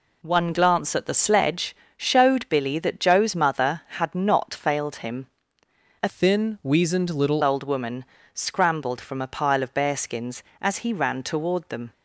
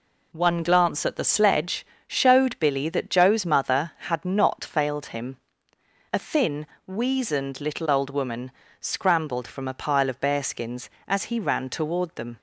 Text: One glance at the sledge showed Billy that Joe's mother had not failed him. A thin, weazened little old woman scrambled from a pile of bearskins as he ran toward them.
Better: second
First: pauses between "sledge" and "showed"; slight; at 1.7 s; 0.22 s long // changes voice from "thin" to "little"; from 6.0 to 7.4 s; 1.4 s long // pauses between "woman" and "scrambled"; slight; at 8.0 s; 0.30 s long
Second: pauses between "sledge" and "showed"; slight; at 1.8 s; 0.22 s long // pauses between "woman" and "scrambled"; slight; at 8.5 s; 0.30 s long

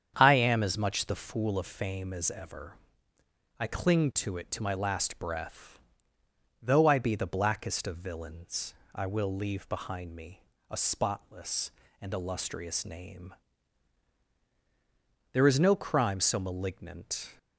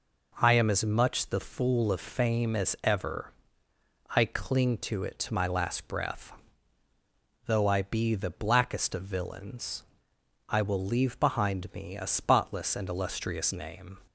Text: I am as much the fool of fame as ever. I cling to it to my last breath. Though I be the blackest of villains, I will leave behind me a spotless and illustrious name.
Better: second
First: starts louder than the rest; strong; until 1.1 s; 8 dB // pauses between "me" and "a"; slight; at 10.4 s; 0.30 s long // goes on to say "There is no crime so malignant"; strong; from 15.3 s on; 2.0 s long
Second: none

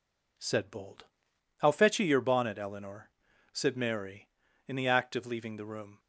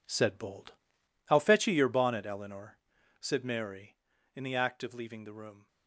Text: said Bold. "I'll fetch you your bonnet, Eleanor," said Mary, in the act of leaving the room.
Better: first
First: none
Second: gets quieter; strong; throughout; 11 dB

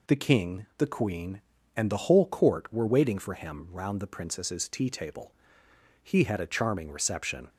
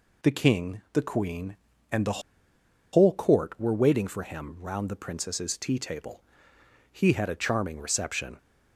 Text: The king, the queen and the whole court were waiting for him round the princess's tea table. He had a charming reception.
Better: first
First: none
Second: pauses between "the" and "whole"; noticeable; at 2.1 s; 0.73 s long

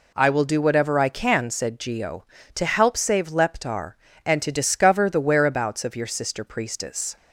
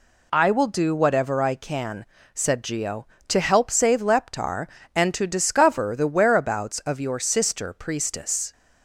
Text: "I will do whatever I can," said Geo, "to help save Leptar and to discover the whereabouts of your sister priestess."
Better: neither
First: none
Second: none

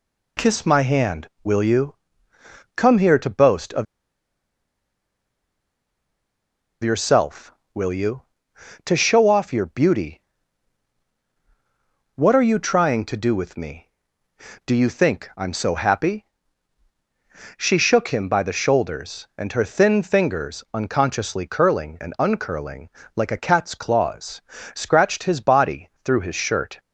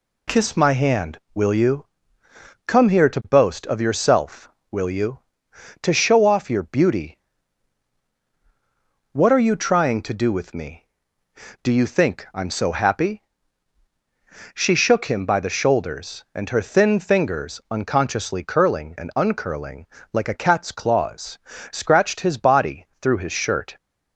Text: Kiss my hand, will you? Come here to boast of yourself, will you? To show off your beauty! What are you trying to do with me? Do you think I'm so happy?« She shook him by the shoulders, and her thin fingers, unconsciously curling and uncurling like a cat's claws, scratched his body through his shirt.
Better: second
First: pauses between "of" and "yourself"; strong; at 3.8 s; 2.9 s long // pauses between "uncurling" and "like"; slight; at 22.8 s; 0.28 s long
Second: pauses between "uncurling" and "like"; slight; at 19.8 s; 0.28 s long

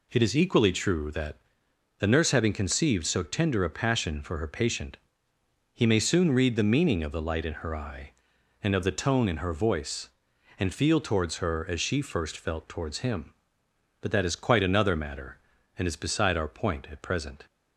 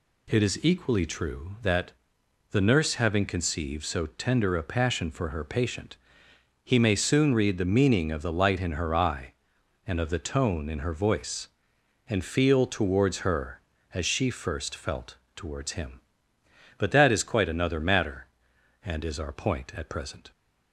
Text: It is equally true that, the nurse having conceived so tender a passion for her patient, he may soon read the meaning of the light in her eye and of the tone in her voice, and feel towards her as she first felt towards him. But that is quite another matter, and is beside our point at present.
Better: first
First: none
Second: pauses between "felt" and "towards"; slight; at 15.1 s; 0.18 s long // skips "beside"; at 19.1 s

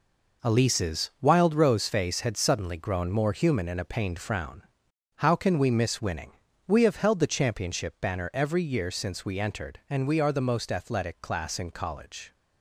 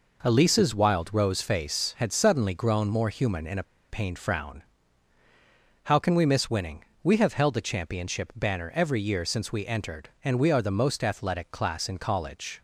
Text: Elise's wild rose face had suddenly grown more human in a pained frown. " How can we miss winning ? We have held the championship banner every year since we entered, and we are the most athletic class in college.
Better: first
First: none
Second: pauses between "a" and "pained"; slight; at 3.6 s; 0.25 s long

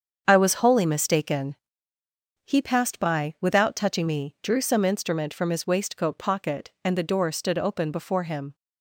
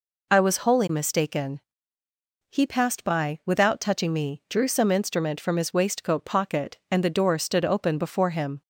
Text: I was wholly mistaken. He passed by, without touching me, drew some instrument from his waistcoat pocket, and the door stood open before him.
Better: second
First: gets quieter; strong; throughout; 9.5 dB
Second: none

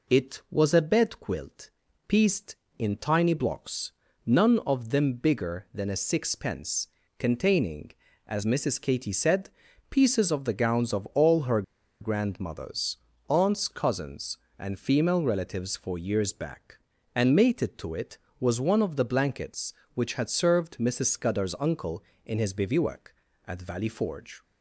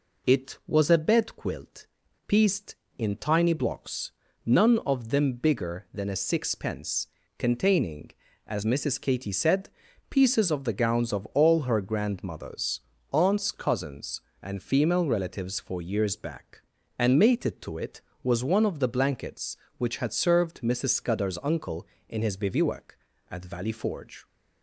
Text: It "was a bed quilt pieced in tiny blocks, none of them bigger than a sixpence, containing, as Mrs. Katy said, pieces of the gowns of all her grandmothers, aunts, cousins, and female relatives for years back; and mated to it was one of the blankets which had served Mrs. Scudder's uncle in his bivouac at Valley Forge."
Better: second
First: pauses between "quilt" and "pieced"; at 1.6 s; 0.38 s long // pauses between "her" and "grandmothers"; at 11.6 s; 0.39 s long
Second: pauses between "quilt" and "pieced"; at 1.8 s; 0.41 s long

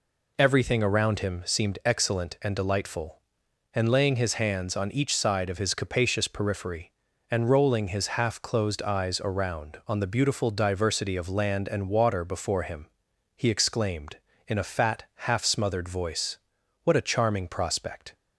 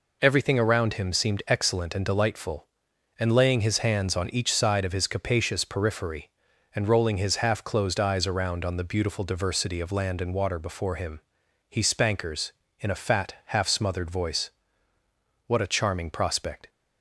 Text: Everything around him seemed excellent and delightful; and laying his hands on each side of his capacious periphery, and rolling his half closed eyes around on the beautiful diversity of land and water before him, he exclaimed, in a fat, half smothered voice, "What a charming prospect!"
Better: first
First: none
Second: says "spankers" for "exclaimed"; at 11.8 s

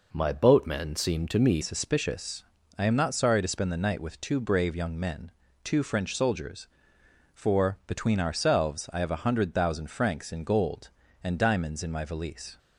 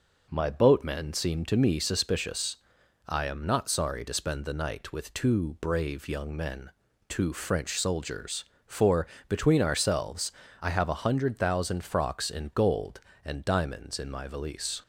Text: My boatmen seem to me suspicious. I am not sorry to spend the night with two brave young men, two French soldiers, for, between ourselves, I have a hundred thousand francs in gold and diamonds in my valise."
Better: second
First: changes voice at "suspicious"; from 1.6 s on; 10.9 s long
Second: none

